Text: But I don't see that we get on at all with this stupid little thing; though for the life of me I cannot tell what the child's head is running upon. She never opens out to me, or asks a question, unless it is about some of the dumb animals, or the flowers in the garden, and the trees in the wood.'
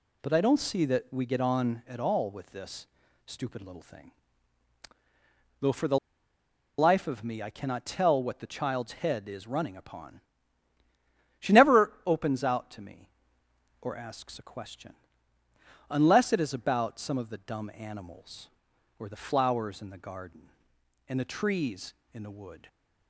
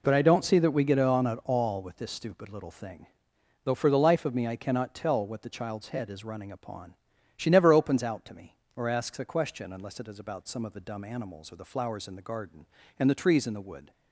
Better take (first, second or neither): second